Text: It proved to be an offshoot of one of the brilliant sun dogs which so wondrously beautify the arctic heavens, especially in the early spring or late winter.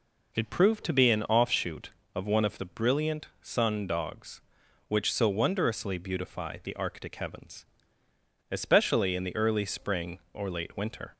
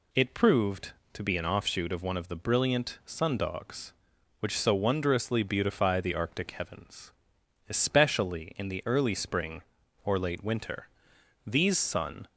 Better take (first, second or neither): first